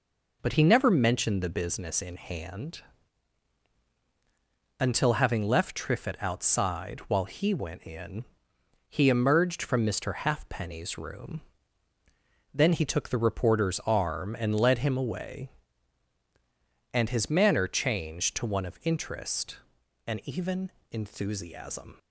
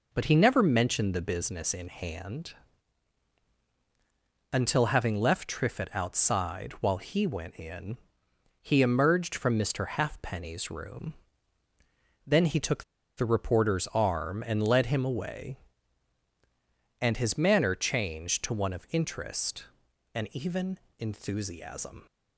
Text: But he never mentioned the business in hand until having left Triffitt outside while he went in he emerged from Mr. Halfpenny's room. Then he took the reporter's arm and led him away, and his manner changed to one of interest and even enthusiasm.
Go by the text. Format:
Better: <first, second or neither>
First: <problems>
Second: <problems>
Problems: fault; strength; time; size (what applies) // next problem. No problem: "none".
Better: first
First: pauses between "hand" and "until"; strong; at 2.8 s; 1.9 s long // pauses between "in" and "he"; noticeable; at 8.2 s; 0.66 s long // pauses between "even" and "enthusiasm"; slight; at 20.7 s; 0.18 s long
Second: pauses between "hand" and "until"; strong; at 2.5 s; 1.9 s long // pauses between "in" and "he"; noticeable; at 7.9 s; 0.66 s long // pauses between "took" and "the"; slight; at 12.8 s; 0.33 s long // pauses between "even" and "enthusiasm"; slight; at 20.7 s; 0.18 s long